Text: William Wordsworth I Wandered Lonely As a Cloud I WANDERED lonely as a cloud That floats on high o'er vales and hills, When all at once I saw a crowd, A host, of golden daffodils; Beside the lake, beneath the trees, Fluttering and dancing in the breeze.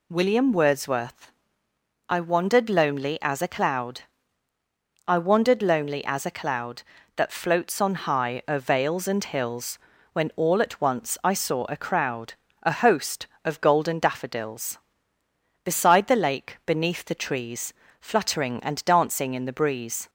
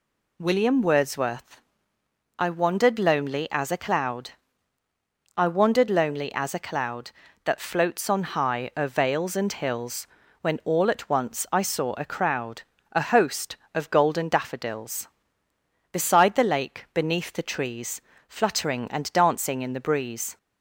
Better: neither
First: pauses between "Wordsworth" and "I"; noticeable; at 1.3 s; 0.78 s long // pauses between "Cloud" and "I"; at 4.0 s; 1.0 s long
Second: pauses between "Wordsworth" and "I"; noticeable; at 1.6 s; 0.78 s long // pauses between "Cloud" and "I"; at 4.3 s; 1.0 s long

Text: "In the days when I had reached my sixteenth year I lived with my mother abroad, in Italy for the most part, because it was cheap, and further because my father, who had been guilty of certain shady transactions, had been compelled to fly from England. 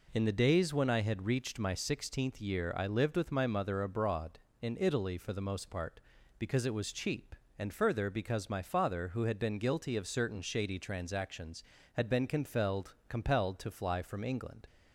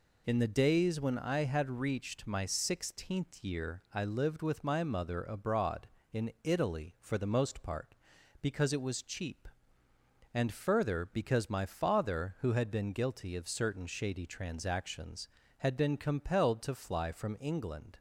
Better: second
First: says "compelled" twice; at 13.0 s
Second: none

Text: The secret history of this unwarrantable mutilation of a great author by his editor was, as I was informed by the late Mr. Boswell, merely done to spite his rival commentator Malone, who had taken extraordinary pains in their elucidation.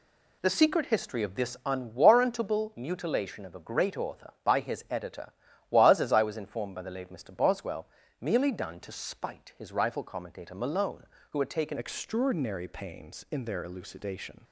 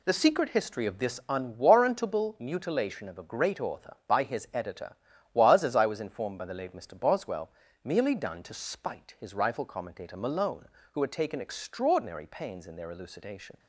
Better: second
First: changes voice at "extraordinary"; from 11.7 s on; 2.7 s long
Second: none

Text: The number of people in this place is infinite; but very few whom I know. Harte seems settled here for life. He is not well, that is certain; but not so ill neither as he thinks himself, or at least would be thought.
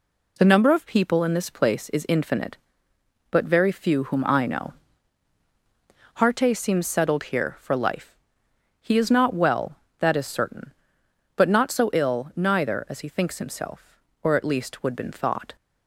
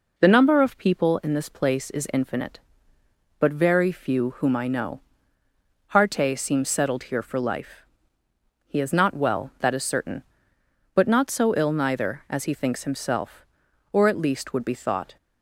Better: second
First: says "been" for "be"; at 14.9 s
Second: none

